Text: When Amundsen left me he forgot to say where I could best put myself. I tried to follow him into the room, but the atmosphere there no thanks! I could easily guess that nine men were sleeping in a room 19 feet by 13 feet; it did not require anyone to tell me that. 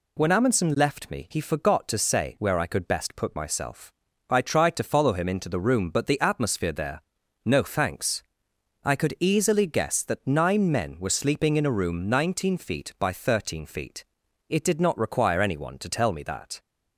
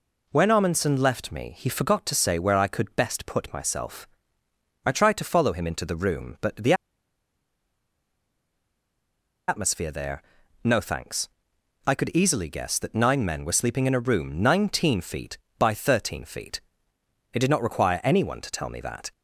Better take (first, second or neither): first